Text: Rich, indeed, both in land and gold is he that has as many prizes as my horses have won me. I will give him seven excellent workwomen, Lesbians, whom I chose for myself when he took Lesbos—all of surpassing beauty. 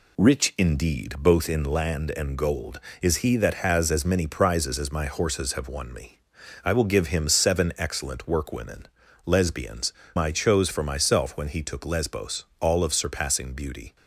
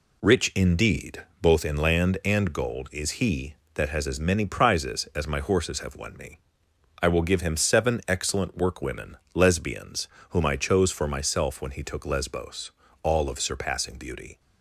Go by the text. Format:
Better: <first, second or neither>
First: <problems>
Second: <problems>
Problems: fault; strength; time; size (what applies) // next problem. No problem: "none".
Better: second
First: skips "whom"; at 10.0 s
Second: none